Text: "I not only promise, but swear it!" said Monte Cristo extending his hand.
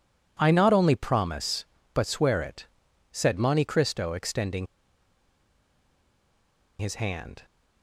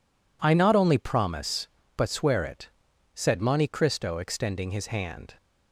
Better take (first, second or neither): second